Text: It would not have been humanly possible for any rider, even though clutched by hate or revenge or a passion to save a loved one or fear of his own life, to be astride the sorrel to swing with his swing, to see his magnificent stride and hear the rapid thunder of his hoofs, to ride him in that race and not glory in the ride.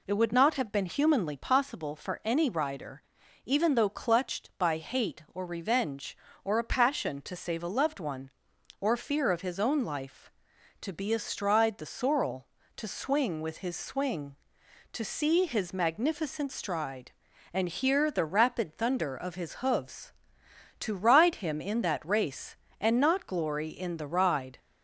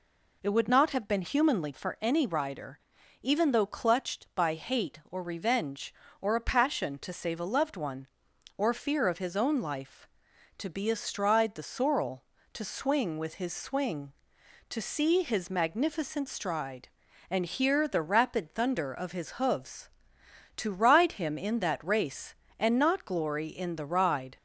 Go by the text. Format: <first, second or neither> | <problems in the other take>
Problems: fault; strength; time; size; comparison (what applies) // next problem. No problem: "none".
first | skips "possible"; at 1.7 s